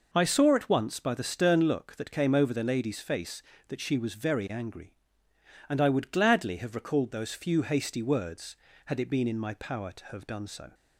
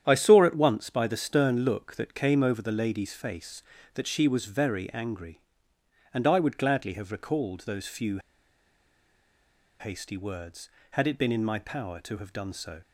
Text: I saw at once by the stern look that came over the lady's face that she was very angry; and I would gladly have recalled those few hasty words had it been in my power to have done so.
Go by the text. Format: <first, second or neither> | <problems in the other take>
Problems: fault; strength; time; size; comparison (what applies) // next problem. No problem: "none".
first | starts louder than the rest; strong; until 1.0 s; 9.5 dB // pauses between "few" and "hasty"; strong; at 8.1 s; 1.6 s long